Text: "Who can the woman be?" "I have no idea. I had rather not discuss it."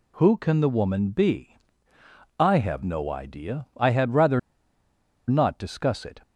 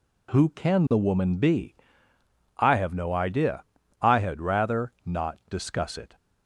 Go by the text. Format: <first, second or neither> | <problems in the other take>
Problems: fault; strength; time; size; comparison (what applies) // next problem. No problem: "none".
second | pauses between "rather" and "not"; noticeable; at 4.3 s; 0.88 s long